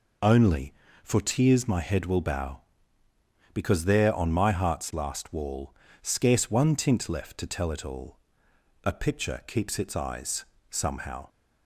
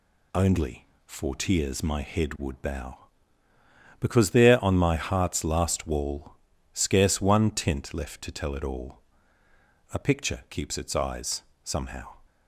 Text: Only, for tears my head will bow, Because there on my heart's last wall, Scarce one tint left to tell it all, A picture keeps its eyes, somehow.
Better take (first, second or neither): first